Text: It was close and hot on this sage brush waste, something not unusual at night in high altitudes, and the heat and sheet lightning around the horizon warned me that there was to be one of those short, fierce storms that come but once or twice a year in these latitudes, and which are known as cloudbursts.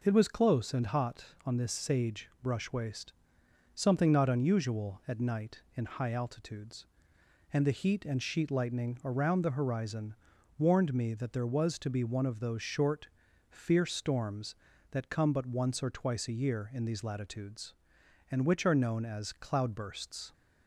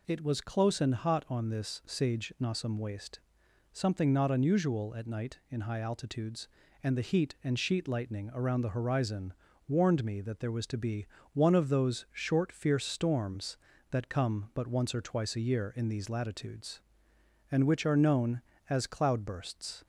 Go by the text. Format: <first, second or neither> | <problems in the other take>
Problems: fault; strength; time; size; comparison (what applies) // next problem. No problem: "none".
first | says "nossum" for "brush"; at 2.3 s // pauses between "horizon" and "warned"; slight; at 9.3 s; 0.34 s long; also in the first // pauses between "be" and "one"; slight; at 11.0 s; 0.26 s long